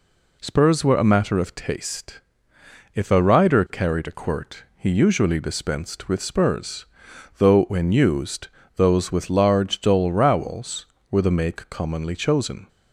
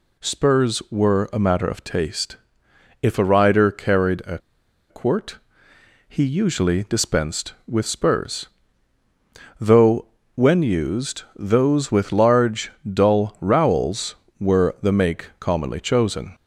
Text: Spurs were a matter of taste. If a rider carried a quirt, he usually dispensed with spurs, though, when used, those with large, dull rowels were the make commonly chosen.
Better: first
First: none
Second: pauses between "a" and "quirt"; noticeable; at 4.3 s; 0.51 s long

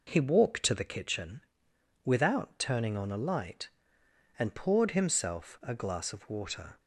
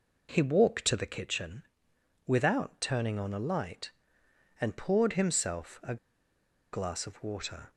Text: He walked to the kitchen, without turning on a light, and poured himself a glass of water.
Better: first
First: none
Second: pauses between "a" and "glass"; noticeable; at 5.9 s; 0.76 s long

